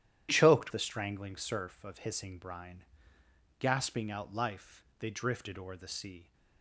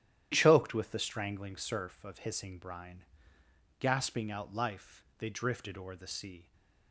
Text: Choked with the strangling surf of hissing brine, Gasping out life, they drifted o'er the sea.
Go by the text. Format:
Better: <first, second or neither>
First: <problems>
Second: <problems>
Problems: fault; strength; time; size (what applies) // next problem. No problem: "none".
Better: second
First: starts louder than the rest; strong; until 1.3 s; 11.5 dB // skips "with"; at 0.7 s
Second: starts louder than the rest; strong; until 1.3 s; 11.5 dB